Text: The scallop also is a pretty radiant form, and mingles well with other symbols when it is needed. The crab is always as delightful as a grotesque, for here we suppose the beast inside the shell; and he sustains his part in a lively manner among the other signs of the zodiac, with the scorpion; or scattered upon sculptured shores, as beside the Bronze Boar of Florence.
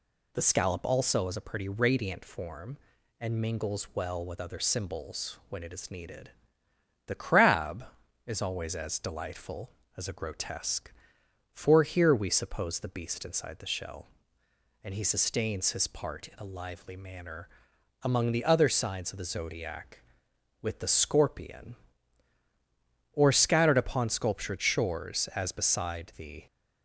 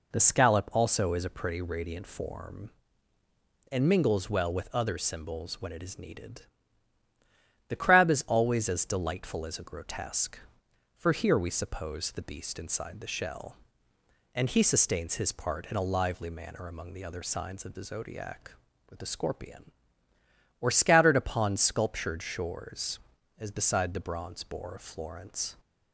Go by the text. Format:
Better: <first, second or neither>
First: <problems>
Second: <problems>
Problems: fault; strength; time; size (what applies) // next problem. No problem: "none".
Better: second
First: pauses between "manner" and "among"; noticeable; at 17.4 s; 0.54 s long // stops before "Bronze Boar of Florence"; at 26.4 s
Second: none